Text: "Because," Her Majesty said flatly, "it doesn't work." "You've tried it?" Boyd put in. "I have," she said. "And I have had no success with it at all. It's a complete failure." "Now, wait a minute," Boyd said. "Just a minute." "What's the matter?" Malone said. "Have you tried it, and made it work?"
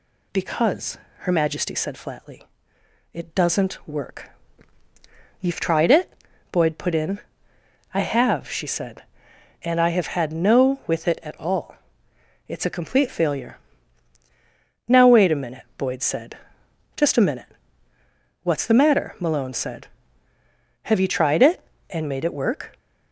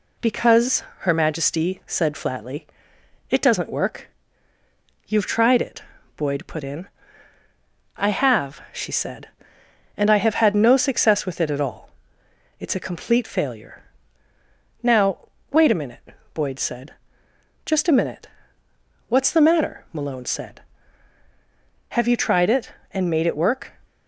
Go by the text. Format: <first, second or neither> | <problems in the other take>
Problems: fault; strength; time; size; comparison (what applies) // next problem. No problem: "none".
second | skips "success"; at 10.8 s